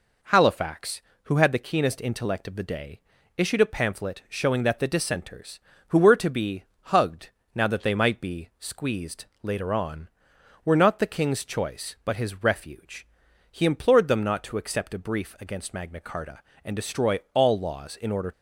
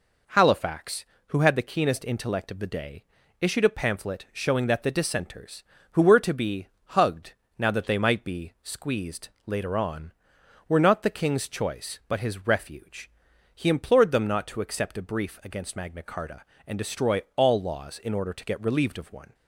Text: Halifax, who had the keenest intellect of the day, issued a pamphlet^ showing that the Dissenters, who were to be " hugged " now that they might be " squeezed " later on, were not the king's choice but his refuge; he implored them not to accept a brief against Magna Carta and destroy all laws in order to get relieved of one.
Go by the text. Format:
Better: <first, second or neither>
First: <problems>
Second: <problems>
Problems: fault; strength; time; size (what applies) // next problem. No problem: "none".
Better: second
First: stops before "to get relieved of one"; at 18.3 s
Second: none